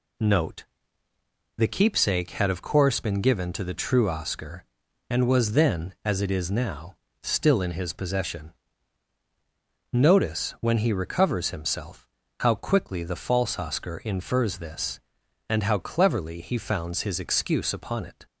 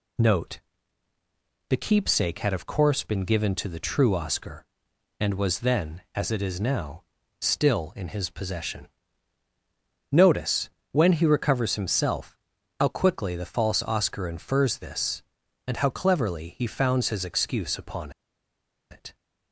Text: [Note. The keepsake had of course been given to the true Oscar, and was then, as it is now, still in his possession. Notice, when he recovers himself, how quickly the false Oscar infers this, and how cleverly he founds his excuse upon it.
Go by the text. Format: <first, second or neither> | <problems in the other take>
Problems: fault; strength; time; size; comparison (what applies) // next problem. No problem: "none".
first | pauses between "upon" and "it"; noticeable; at 18.1 s; 0.80 s long